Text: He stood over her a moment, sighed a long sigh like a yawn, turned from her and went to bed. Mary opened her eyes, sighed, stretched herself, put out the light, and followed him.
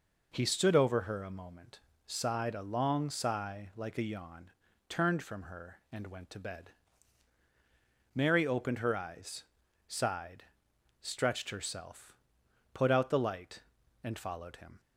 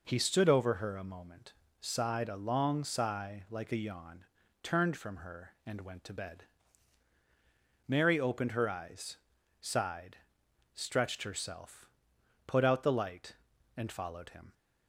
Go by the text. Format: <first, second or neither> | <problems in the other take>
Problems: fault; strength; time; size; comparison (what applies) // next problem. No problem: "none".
neither | none